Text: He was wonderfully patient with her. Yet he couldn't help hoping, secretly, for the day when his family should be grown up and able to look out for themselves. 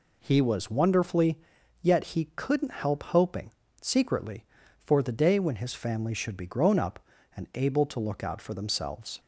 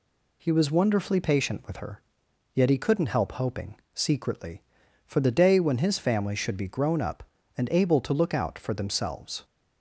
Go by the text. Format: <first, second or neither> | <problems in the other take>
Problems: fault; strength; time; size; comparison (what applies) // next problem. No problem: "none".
second | skips "patient with her"; at 1.5 s